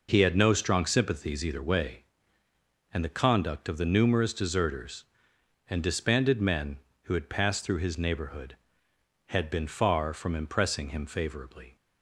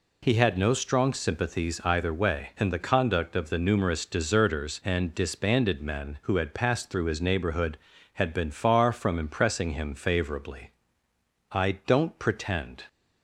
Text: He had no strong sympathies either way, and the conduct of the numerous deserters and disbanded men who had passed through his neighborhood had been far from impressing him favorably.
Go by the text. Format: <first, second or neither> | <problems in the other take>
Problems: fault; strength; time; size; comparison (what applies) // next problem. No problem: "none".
first | goes on to say "I don't pretend"; from 11.5 s on; 1.3 s long